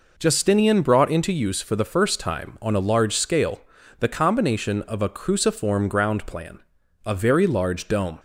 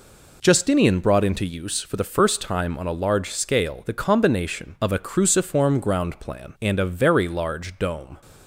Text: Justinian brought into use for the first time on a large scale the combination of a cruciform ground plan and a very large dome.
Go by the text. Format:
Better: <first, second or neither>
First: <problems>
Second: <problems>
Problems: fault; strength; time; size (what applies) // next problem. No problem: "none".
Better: second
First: pauses between "scale" and "the"; at 3.6 s; 0.38 s long // skips "and"; at 6.8 s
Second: none